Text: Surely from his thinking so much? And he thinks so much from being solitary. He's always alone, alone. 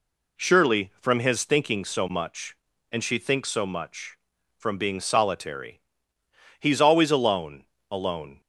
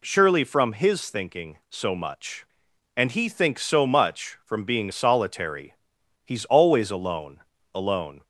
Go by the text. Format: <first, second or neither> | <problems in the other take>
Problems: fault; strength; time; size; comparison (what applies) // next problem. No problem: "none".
second | says "she" for "he"; at 3.0 s